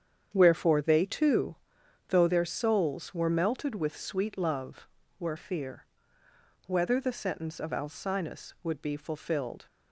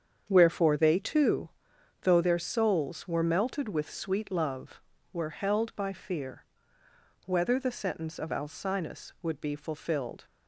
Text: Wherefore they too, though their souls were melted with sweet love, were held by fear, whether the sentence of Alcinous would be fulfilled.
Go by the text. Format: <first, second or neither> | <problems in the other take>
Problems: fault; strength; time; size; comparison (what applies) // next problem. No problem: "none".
second | starts louder than the rest; strong; until 1.3 s; 8 dB; strong in the second // skips "held by"; at 5.3 s